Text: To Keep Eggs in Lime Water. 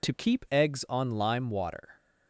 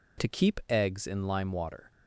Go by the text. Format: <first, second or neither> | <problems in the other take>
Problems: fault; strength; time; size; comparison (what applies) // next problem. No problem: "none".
second | says "on" for "in"; at 0.8 s